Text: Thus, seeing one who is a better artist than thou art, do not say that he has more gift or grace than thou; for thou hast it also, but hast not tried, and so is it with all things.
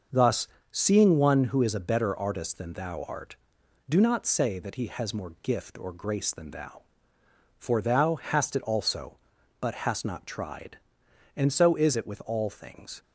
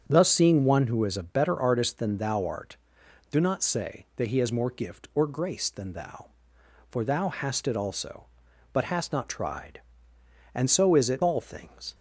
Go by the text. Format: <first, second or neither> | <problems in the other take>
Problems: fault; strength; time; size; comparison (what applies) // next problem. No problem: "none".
first | starts louder than the rest; strong; until 1.1 s; 7.5 dB; also in the first // skips "with"; at 11.2 s